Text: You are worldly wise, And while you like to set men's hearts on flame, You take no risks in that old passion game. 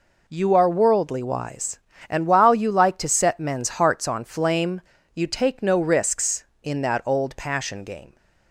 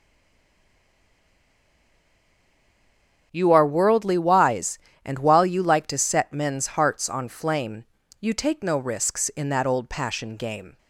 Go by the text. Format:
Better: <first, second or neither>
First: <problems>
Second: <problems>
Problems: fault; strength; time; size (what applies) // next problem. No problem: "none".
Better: first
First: none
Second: stays silent before the first word; strong; until 3.3 s; 3.3 s long // starts louder than the rest; until 4.3 s; 7 dB